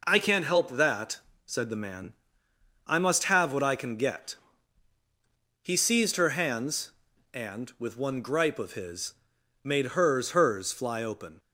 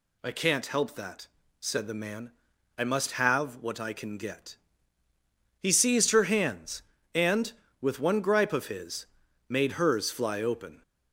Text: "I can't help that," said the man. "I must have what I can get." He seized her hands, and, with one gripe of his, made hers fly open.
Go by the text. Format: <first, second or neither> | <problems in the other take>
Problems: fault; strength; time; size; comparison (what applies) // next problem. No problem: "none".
second | says "hers" twice; at 10.3 s